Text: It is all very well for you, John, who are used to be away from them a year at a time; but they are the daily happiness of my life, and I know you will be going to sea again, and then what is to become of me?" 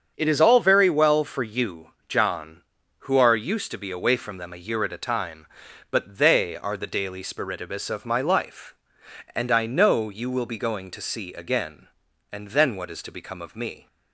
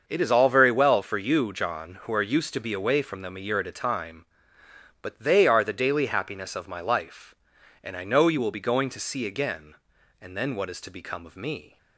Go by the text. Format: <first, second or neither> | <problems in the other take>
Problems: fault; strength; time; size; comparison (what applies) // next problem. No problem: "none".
second | starts louder than the rest; strong; until 1.1 s; 7 dB; also in the second // says "spiritibus" for "happiness"; at 7.2 s